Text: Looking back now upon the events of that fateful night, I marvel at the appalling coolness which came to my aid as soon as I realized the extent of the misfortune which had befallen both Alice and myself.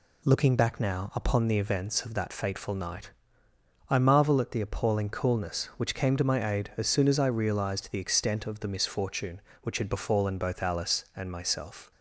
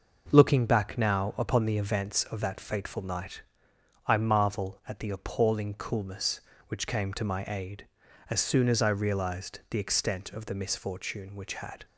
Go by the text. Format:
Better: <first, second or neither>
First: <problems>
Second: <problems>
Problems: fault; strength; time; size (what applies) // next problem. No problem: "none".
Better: first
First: none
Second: stops before "befallen both Alice and myself"; at 11.8 s